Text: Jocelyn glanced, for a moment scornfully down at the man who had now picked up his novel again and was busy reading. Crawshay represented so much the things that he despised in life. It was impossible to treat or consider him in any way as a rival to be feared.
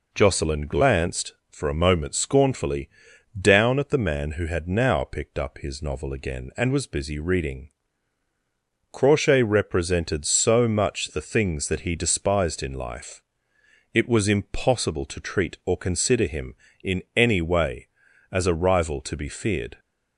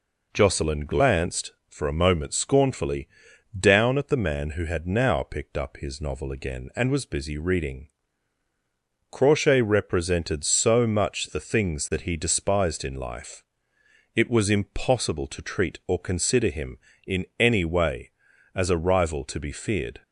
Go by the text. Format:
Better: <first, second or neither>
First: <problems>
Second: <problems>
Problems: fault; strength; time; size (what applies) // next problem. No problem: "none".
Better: neither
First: pauses between "scornfully" and "down"; noticeable; at 2.8 s; 0.50 s long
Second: pauses between "scornfully" and "down"; noticeable; at 3.0 s; 0.50 s long